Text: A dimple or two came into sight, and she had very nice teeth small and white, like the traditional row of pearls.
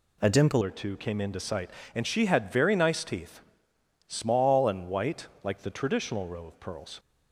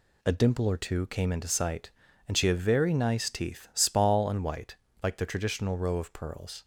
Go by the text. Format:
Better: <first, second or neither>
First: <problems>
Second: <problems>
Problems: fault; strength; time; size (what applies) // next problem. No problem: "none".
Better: second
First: changes voice at "or"; from 0.6 s on; 6.3 s long // pauses between "teeth" and "small"; noticeable; at 3.4 s; 0.70 s long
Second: none